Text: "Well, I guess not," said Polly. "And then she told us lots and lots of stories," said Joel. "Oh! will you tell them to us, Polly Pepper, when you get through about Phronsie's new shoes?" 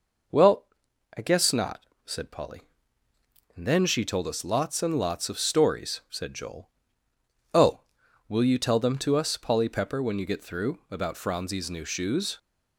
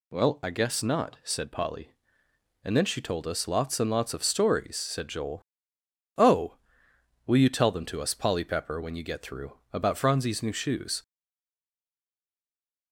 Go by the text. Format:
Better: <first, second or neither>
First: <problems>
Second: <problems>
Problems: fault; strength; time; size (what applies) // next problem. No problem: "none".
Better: first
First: none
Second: stays silent after the last word; noticeable; from 11.0 s on; 1.9 s long